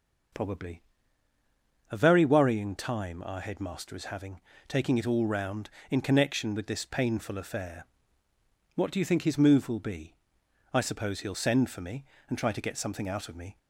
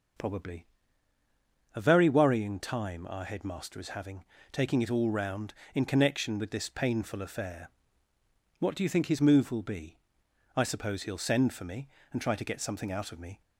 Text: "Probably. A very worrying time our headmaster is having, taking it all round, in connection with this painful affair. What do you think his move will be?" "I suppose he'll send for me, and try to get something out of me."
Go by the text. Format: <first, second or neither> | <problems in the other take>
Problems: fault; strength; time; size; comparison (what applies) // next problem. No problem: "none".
neither | starts louder than the rest; the same in both